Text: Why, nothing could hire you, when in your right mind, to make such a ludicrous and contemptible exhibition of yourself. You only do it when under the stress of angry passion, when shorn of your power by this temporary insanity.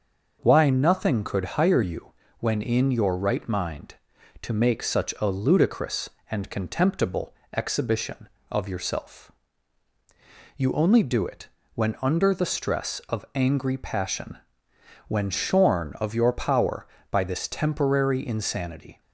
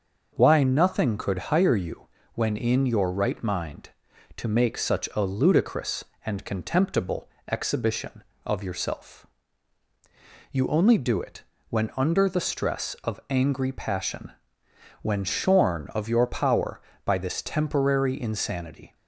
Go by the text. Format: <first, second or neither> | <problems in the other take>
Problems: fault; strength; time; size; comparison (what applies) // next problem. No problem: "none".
neither | starts louder than the rest; the same in both // pauses between "contemptible" and "exhibition"; slight; the same in both // pauses between "it" and "when"; slight; the same in both